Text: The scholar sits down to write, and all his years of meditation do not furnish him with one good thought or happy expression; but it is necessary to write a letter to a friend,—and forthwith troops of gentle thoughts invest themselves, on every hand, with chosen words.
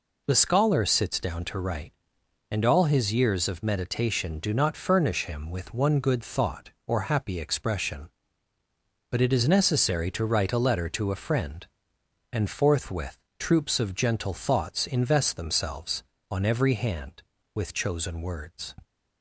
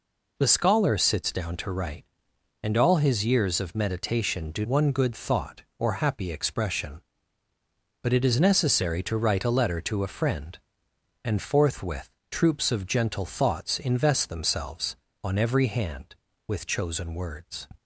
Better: first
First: pauses between "forthwith" and "troops"; slight; at 13.1 s; 0.20 s long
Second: skips "not furnish him with"; at 4.6 s // pauses between "forthwith" and "troops"; slight; at 12.0 s; 0.20 s long

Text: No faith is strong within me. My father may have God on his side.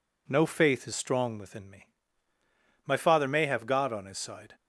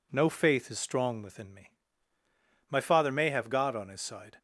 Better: neither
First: none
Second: none

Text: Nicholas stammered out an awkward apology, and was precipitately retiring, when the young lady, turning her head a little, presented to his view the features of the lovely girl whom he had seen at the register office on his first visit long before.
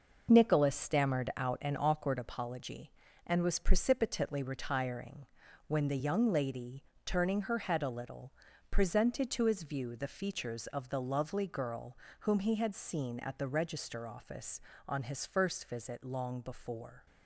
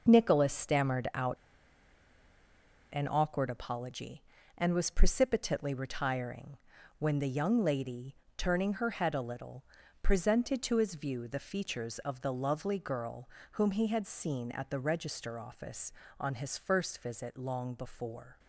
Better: first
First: pauses between "girl" and "whom"; slight; at 11.9 s; 0.22 s long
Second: pauses between "out" and "an"; strong; at 1.3 s; 1.5 s long // pauses between "girl" and "whom"; slight; at 13.2 s; 0.22 s long

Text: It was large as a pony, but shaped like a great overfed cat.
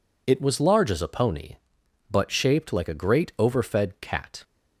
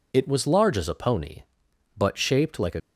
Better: first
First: none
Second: stops before "great overfed cat"; at 2.7 s

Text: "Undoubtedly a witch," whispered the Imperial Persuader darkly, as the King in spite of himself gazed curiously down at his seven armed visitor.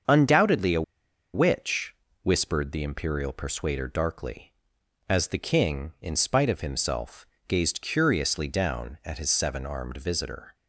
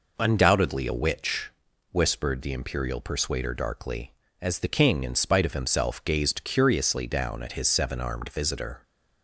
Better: second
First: starts louder than the rest; until 1.6 s; 7 dB // pauses between "a" and "witch"; noticeable; at 0.8 s; 0.52 s long // pauses between "himself" and "gazed"; slight; at 7.2 s; 0.22 s long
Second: none

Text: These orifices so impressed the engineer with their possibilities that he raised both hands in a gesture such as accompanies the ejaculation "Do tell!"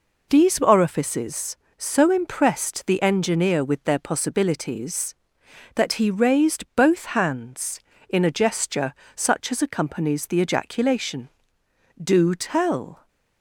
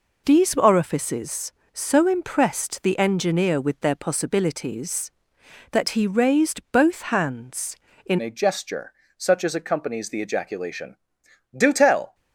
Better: first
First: pauses between "gesture" and "such"; slight; at 8.9 s; 0.22 s long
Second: changes voice at "a"; from 8.2 s on; 3.9 s long // pauses between "gesture" and "such"; slight; at 8.9 s; 0.24 s long

